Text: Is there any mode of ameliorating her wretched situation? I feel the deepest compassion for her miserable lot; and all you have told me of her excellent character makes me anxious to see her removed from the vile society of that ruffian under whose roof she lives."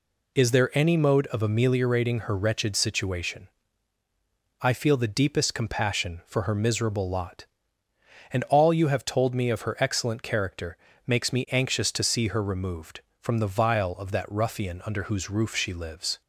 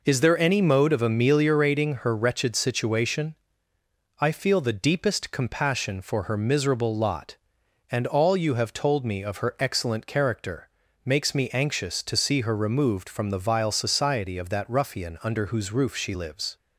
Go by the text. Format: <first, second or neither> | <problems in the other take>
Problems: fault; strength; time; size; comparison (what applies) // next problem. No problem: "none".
second | pauses between "character" and "makes"; slight; at 10.7 s; 0.30 s long; also in the second // skips "society"; at 13.9 s